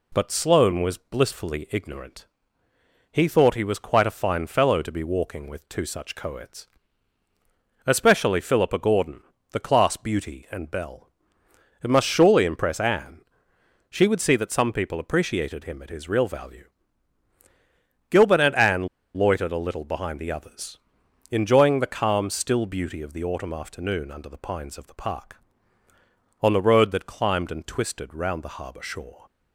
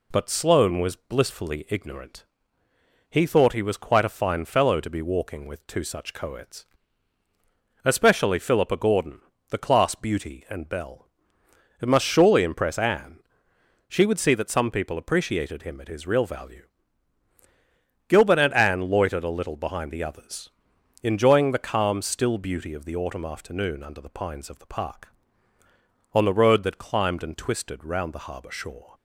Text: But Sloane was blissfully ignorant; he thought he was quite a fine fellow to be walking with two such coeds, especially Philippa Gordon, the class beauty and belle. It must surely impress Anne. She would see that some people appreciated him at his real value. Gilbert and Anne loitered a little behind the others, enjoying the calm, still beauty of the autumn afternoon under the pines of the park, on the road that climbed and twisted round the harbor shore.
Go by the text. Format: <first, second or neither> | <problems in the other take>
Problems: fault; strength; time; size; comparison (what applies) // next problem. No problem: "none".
second | pauses between "Anne" and "loitered"; slight; at 18.8 s; 0.29 s long